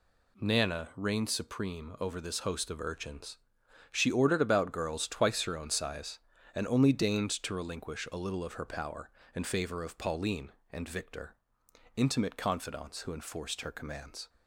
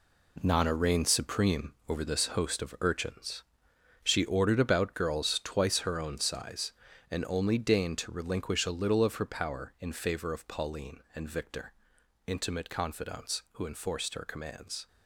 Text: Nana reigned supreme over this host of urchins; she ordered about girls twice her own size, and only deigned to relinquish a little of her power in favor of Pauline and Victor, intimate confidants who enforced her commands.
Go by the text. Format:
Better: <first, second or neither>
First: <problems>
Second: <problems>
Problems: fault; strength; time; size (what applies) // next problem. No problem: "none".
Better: first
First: none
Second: gets quieter; strong; throughout; 9.5 dB // pauses between "supreme" and "over"; slight; at 1.7 s; 0.16 s long